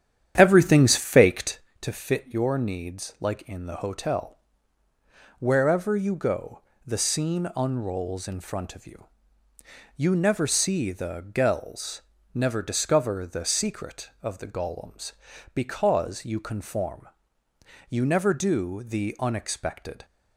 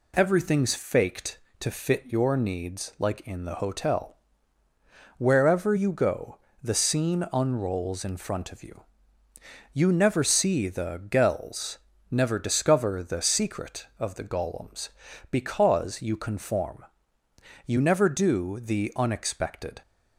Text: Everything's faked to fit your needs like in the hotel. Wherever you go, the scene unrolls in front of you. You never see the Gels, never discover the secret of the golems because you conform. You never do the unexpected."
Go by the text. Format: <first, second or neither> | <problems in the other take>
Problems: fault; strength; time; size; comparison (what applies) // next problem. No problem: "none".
second | starts louder than the rest; strong; until 1.7 s; 9.5 dB